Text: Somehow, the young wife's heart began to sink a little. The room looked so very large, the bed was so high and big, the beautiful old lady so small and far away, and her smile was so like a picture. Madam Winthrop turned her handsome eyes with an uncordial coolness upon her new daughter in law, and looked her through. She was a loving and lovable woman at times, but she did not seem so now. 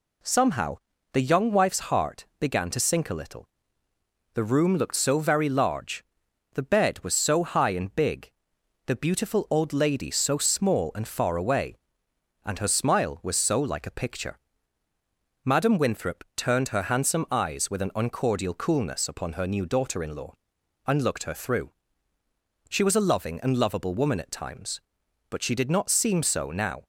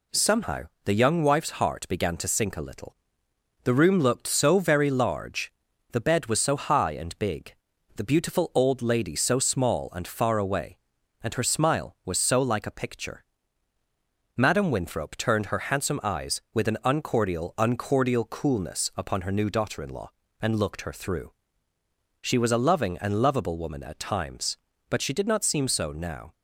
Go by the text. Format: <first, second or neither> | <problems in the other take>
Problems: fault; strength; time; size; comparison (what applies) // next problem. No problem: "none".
first | says "uncordial" twice; at 17.5 s